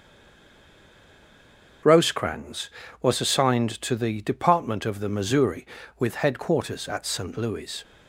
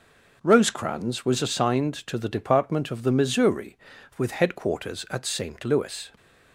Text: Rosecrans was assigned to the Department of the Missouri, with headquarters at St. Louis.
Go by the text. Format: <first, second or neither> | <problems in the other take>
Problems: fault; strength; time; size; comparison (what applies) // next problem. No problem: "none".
second | stays silent before the first word; noticeable; until 1.8 s; 1.8 s long // starts louder than the rest; until 3.1 s; 6.5 dB